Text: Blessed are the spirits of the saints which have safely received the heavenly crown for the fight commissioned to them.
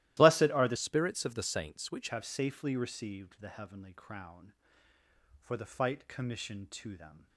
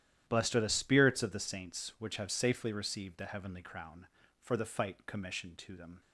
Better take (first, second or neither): second